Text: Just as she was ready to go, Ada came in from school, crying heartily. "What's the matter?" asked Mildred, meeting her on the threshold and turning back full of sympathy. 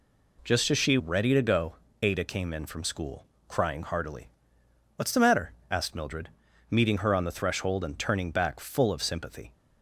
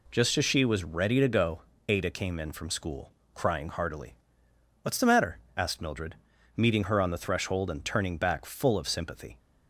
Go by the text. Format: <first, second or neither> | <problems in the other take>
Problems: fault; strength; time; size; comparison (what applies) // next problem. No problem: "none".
second | skips "was"; at 0.9 s